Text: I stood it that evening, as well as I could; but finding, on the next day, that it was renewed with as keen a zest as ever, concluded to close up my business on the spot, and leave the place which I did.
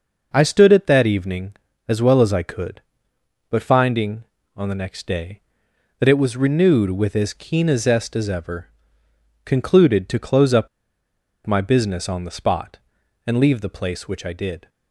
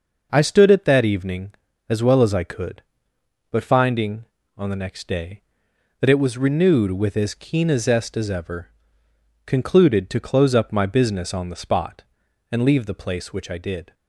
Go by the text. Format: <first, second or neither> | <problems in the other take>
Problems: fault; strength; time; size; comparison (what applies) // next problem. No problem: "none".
second | pauses between "up" and "my"; noticeable; at 10.6 s; 0.78 s long